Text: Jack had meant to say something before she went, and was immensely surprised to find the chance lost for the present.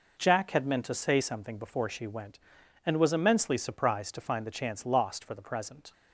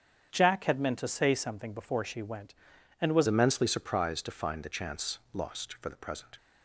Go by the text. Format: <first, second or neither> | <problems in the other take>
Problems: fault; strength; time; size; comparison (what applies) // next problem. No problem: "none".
first | starts louder than the rest; strong; until 1.3 s; 8 dB // changes voice at "immensely"; from 3.2 s on; 3.1 s long